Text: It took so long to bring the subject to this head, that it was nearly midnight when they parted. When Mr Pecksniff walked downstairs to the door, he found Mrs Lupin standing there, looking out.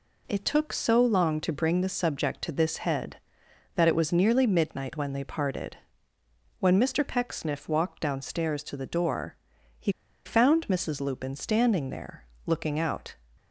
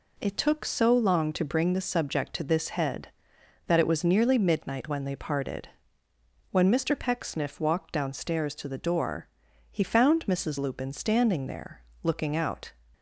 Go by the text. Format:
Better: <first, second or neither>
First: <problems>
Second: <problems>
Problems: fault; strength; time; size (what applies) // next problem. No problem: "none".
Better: second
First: pauses between "he" and "found"; slight; at 9.9 s; 0.33 s long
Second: none